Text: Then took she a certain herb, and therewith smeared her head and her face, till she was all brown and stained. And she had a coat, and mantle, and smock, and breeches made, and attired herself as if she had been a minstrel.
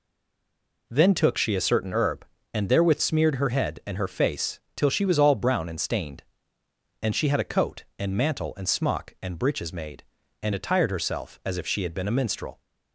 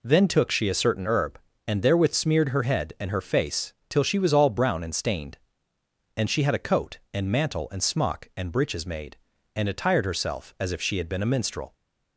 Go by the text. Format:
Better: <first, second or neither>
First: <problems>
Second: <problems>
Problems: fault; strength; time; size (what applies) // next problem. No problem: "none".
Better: second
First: stays silent before the first word; slight; until 0.8 s; 0.8 s long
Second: none